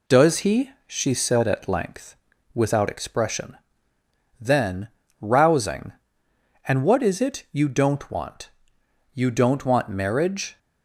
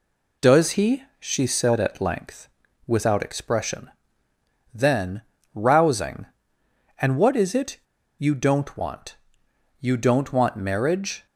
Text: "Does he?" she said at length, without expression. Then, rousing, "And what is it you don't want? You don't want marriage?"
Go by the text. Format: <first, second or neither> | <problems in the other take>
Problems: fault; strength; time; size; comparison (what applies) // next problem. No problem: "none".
first | pauses between "it" and "you"; at 7.7 s; 0.41 s long